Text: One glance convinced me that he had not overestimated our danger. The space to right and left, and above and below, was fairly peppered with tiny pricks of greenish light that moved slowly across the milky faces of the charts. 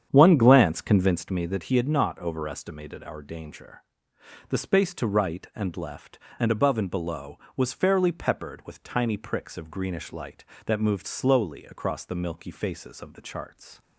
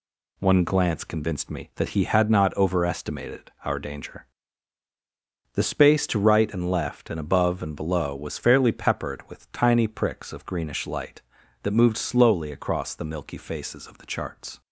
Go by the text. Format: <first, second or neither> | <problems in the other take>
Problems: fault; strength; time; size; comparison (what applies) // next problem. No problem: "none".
second | starts louder than the rest; strong; until 1.3 s; 8.5 dB